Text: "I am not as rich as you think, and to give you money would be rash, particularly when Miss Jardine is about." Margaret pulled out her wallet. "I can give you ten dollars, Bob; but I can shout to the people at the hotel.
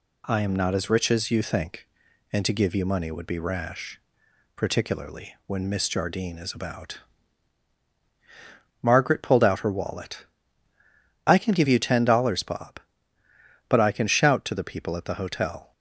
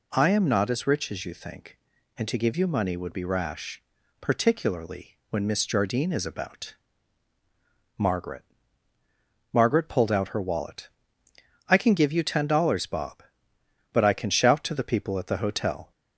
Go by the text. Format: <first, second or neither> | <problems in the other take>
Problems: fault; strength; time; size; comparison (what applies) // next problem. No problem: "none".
first | says "Margaret" twice; at 9.5 s